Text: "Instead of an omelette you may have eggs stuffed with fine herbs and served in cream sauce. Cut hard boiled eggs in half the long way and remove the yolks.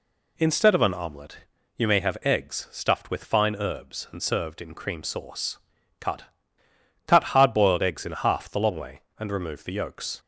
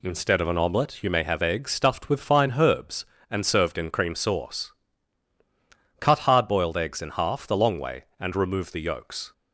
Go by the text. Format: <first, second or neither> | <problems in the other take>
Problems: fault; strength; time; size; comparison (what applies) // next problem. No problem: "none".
second | pauses between "omelette" and "you"; at 1.3 s; 0.40 s long // says "Cut" twice; at 7.0 s